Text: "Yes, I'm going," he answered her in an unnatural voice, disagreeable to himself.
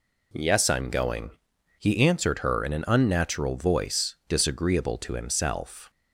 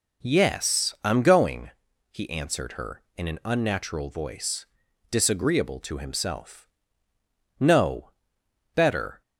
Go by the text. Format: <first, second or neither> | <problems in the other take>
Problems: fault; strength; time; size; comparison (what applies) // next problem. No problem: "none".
first | goes on to say "No better"; from 7.5 s on; 1.6 s long